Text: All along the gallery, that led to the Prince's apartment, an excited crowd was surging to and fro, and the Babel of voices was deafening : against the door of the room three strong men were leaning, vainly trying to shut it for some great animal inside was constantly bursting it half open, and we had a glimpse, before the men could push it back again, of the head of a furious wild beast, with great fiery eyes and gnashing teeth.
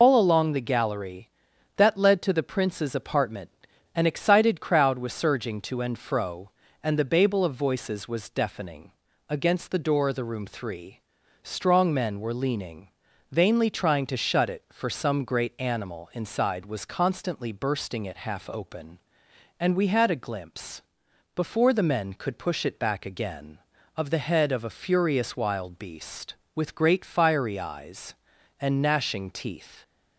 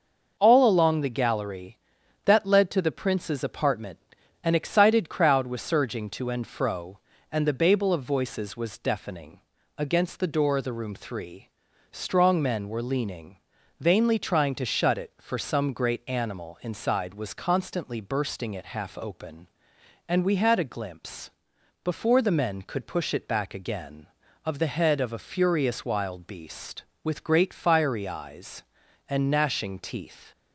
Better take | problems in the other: second | loses the start of "All"; at 0.0 s; 100 ms // pauses between "three" and "strong"; noticeable; at 10.9 s; 0.46 s long; noticeable in the second

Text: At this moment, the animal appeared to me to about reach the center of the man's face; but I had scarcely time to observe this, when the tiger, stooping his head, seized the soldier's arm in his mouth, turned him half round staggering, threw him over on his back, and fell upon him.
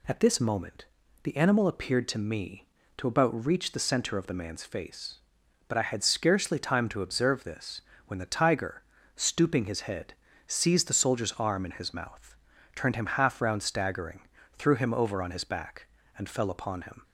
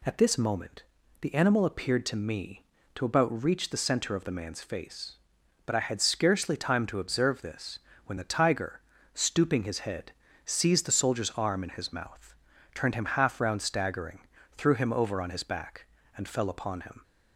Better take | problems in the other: neither | none

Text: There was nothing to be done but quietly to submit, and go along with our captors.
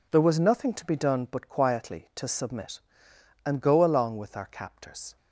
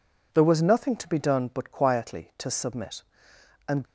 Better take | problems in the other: first | stops before "go along with our captors"; at 3.8 s

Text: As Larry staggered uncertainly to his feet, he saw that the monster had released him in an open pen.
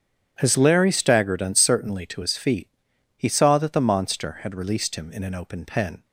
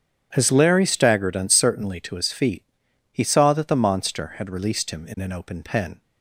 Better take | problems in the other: neither | starts louder than the rest; strong; the same in both

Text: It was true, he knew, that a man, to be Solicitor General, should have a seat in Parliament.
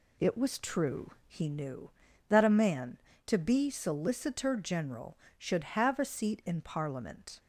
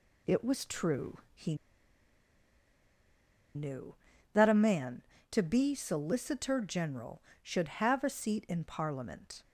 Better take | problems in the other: first | pauses between "he" and "knew"; strong; at 1.5 s; 2.0 s long

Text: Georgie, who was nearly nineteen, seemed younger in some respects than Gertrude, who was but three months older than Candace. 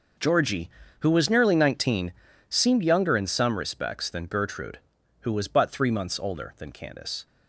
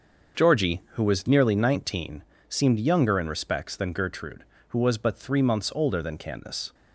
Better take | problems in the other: first | starts louder than the rest; until 1.4 s; 6.5 dB // skips "some"; at 3.2 s

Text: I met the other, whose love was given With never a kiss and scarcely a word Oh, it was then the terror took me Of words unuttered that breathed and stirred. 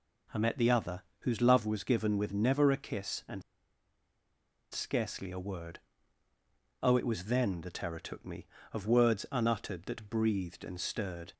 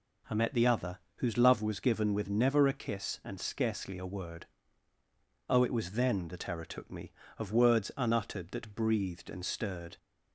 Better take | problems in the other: second | pauses between "and" and "scarcely"; strong; at 3.4 s; 1.2 s long // pauses between "word" and "Oh"; at 5.7 s; 1.0 s long; also in the second

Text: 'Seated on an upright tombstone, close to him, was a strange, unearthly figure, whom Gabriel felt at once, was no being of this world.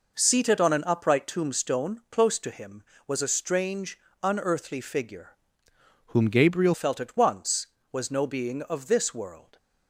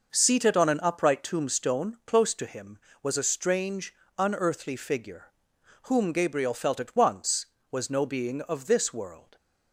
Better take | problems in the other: second | changes voice from "whom" to "Gabriel"; from 6.0 to 6.7 s; 0.7 s long

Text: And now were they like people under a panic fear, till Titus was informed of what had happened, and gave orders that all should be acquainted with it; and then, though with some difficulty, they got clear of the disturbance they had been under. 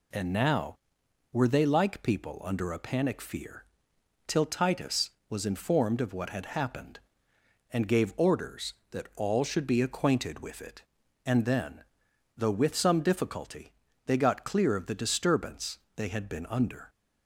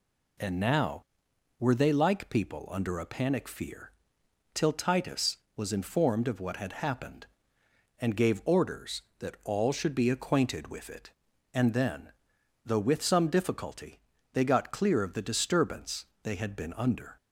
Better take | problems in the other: neither | pauses between "disturbance" and "they"; slight; the same in both

